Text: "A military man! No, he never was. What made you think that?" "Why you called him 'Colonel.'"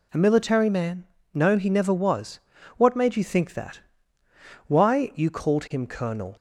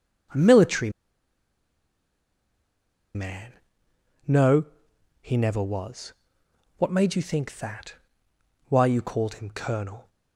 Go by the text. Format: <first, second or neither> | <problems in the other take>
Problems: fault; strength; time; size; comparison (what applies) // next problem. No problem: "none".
first | pauses between "military" and "man"; strong; at 0.8 s; 2.2 s long